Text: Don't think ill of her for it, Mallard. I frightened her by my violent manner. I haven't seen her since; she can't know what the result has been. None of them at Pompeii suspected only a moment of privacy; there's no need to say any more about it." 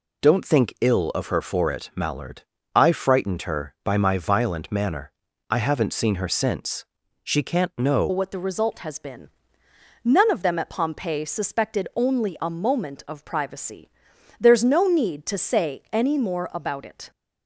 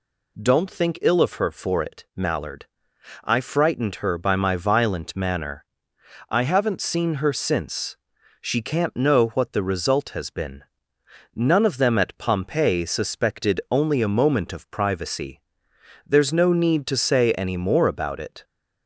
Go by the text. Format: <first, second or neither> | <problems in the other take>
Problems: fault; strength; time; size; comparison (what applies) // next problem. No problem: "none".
second | changes voice at "what"; from 8.0 s on; 9.1 s long